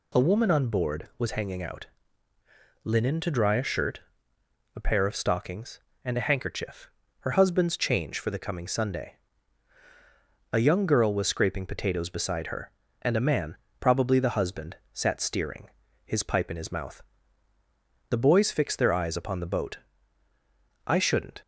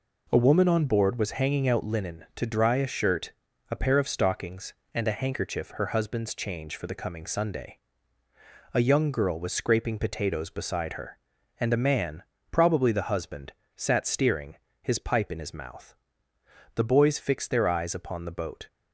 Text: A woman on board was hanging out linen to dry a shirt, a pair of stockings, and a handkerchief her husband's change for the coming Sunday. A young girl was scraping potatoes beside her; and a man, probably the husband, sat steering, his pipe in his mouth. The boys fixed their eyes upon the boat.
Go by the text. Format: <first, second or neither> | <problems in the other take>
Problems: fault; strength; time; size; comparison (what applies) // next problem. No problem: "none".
second | pauses between "out" and "linen"; noticeable; at 1.8 s; 0.96 s long // pauses between "handkerchief" and "her"; slight; at 6.9 s; 0.30 s long // goes on to say "I shouldn't"; from 20.8 s on; 0.56 s long